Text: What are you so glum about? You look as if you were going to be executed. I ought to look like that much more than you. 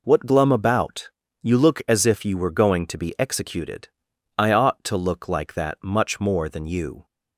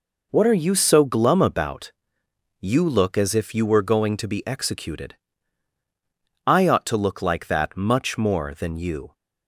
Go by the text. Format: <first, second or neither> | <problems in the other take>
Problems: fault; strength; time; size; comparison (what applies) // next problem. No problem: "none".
second | skips "are you so"; at 0.2 s